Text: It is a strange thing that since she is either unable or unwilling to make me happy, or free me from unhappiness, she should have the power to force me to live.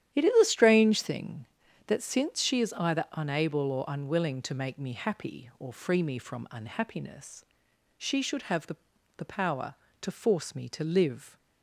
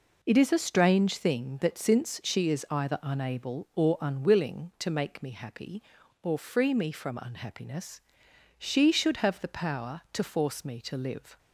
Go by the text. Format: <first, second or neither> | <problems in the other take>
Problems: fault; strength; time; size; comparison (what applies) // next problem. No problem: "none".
second | starts louder than the rest; strong; until 1.2 s; 10 dB // says "the" twice; at 9.1 s